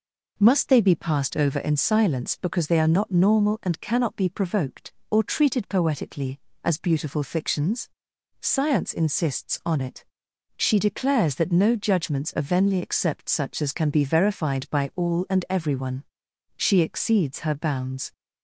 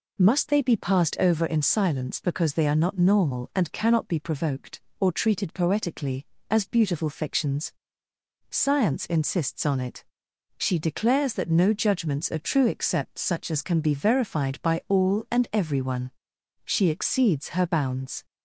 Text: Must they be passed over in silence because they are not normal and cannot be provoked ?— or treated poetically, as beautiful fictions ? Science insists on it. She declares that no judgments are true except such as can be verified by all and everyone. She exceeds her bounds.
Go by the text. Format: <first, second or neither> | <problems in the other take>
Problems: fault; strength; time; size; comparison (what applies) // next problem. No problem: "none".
second | says "venly" for "true"; at 12.4 s